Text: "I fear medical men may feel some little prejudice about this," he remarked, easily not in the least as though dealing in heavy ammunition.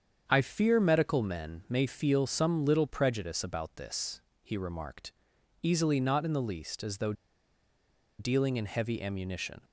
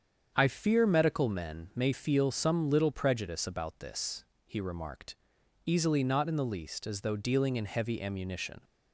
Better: second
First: starts louder than the rest; strong; until 1.2 s; 7.5 dB // pauses between "though" and "dealing"; at 7.1 s; 1.0 s long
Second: starts louder than the rest; strong; until 1.3 s; 7.5 dB

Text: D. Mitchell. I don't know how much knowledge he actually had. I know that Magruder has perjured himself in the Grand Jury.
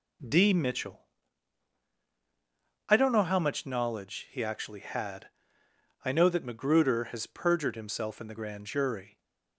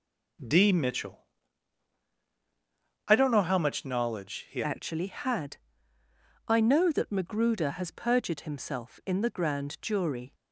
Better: first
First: none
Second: changes voice at "actually"; from 4.6 s on; 5.7 s long

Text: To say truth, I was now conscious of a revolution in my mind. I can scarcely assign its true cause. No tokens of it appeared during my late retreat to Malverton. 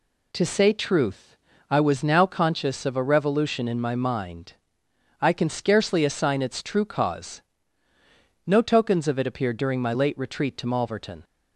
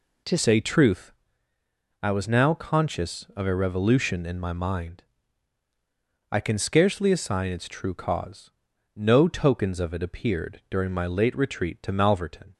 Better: first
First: none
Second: changes voice at "say"; from 0.3 s on; 12.2 s long

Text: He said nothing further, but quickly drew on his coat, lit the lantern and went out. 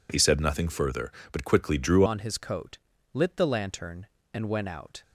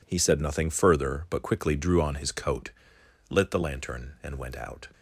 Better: second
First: changes voice at "on"; from 2.0 s on; 3.0 s long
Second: none

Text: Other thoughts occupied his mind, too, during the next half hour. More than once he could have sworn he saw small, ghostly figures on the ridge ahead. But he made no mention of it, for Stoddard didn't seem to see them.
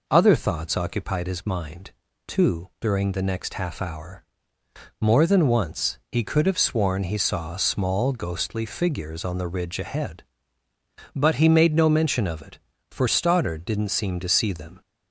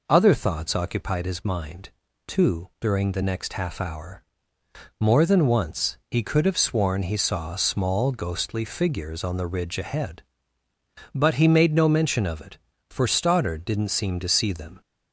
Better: neither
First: none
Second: none

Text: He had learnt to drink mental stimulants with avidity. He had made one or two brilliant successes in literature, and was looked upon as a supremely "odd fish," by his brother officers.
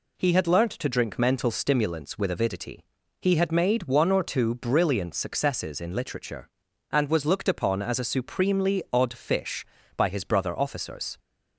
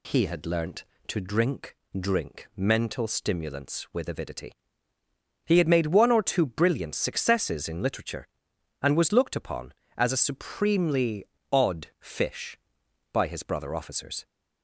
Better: first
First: none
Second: says "drink" twice; at 1.9 s // pauses between "supremely" and "odd"; slight; at 11.2 s; 0.28 s long

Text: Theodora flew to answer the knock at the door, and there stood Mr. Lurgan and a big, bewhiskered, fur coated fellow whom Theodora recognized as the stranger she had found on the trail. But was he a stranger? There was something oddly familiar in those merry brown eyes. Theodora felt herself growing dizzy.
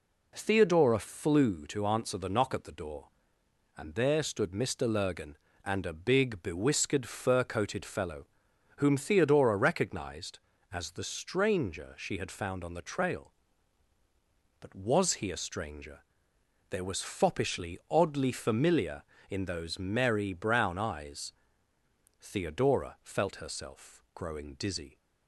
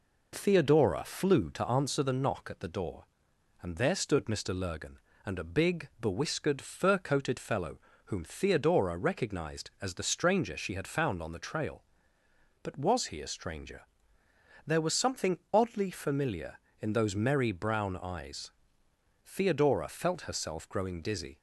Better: second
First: pauses between "fellow" and "whom"; noticeable; at 8.2 s; 0.52 s long // says "foppishly" for "something"; at 17.0 s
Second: pauses between "fellow" and "whom"; slight; at 7.7 s; 0.26 s long

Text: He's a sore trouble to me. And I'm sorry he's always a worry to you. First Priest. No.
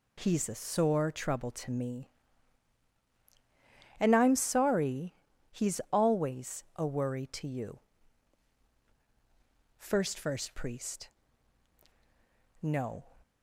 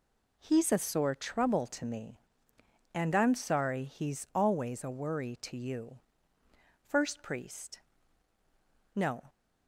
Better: second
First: pauses between "sorry" and "he's"; at 5.1 s; 0.38 s long // says "First" twice; at 10.1 s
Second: none

